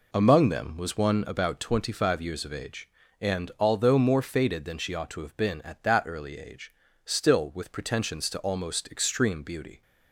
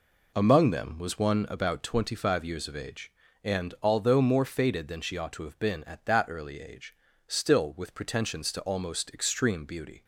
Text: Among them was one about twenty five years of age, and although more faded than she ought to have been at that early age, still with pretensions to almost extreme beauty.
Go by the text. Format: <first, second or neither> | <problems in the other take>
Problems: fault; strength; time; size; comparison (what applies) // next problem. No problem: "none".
neither | none